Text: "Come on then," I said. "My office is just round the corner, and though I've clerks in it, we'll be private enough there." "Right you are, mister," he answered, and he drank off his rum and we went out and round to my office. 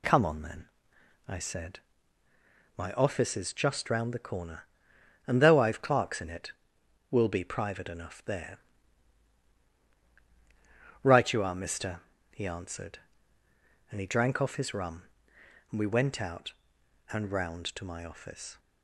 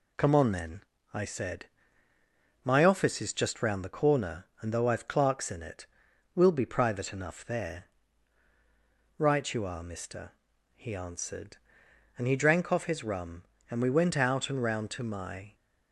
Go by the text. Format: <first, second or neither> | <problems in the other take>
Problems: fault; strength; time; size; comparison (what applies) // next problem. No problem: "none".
first | stops before "office"; at 15.5 s